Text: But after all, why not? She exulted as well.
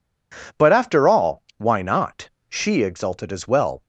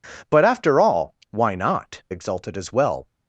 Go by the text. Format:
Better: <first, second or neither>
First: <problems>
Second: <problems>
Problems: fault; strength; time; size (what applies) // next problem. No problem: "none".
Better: first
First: none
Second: skips "She"; at 2.0 s